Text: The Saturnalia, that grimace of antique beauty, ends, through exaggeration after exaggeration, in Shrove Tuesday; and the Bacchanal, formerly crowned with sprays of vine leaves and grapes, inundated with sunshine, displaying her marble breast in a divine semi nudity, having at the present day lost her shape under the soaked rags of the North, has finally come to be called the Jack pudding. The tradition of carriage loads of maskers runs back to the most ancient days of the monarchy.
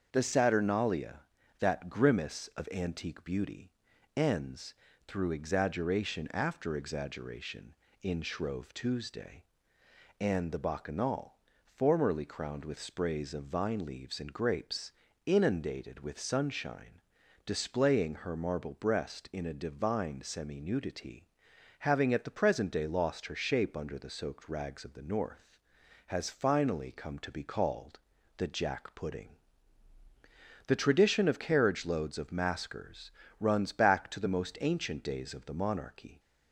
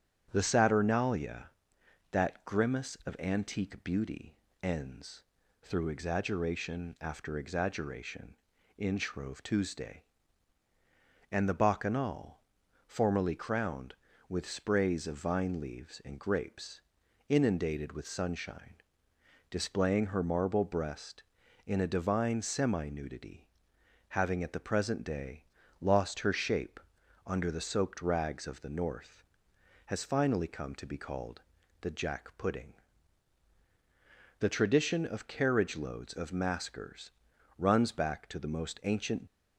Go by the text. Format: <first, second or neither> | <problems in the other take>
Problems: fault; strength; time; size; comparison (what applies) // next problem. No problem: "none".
first | starts louder than the rest; strong; until 1.3 s; 9 dB; also in the first // pauses between "day" and "lost"; slight; at 25.4 s; 0.36 s long // pauses between "shape" and "under"; noticeable; at 26.7 s; 0.46 s long // pauses between "called" and "the"; at 31.4 s; 0.40 s long; also in the first // pauses between "maskers" and "runs"; noticeable; at 37.0 s; 0.48 s long; slight in the first // stops before "days of the monarchy"; at 39.2 s